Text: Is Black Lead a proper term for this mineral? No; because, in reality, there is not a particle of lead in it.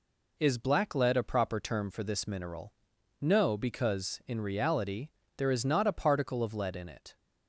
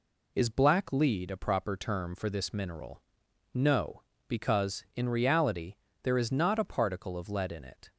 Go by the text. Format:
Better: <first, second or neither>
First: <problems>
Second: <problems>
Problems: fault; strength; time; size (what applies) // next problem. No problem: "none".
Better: neither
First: none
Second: none